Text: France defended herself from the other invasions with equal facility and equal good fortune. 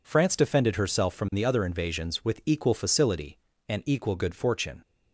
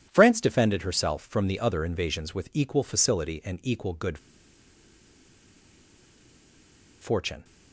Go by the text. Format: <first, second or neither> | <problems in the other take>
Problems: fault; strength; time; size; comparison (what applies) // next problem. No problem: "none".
first | pauses between "good" and "fortune"; strong; at 4.1 s; 2.8 s long